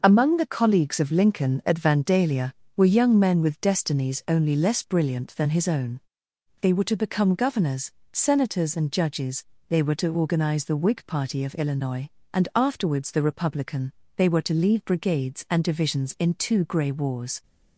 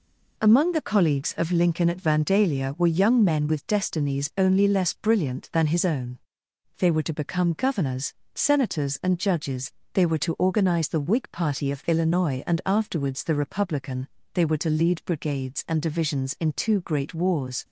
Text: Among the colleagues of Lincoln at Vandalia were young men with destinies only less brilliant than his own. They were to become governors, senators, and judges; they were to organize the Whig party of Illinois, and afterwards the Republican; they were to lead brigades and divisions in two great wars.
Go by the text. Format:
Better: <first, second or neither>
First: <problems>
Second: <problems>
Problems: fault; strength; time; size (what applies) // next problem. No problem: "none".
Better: second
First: starts louder than the rest; until 1.0 s; 6 dB // says "grey" for "great"; at 16.6 s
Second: none